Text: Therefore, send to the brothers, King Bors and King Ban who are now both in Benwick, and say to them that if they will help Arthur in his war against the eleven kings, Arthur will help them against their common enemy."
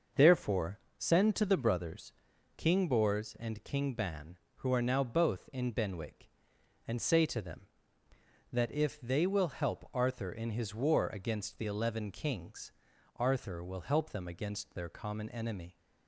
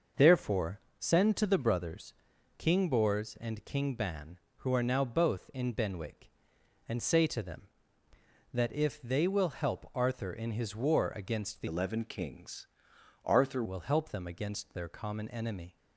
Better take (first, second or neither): first